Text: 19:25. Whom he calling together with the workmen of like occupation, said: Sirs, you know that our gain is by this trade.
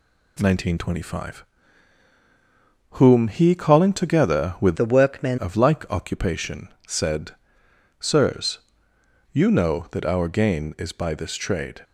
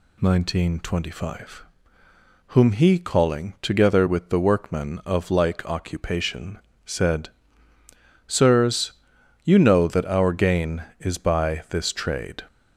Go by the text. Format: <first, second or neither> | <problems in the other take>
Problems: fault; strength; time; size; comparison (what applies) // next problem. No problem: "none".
second | changes voice from "the" to "workmen"; from 4.7 to 5.3 s; 0.6 s long